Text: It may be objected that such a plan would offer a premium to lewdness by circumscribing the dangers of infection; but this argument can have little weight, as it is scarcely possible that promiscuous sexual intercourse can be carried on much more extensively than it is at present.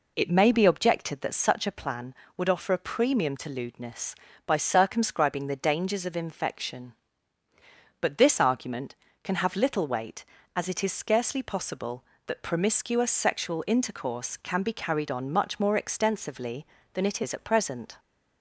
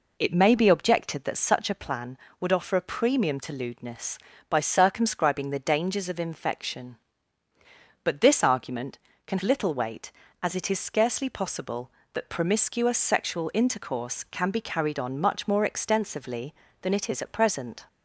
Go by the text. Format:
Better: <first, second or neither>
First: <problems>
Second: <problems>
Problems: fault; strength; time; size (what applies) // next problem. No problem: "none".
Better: first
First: none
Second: skips "have"; at 9.4 s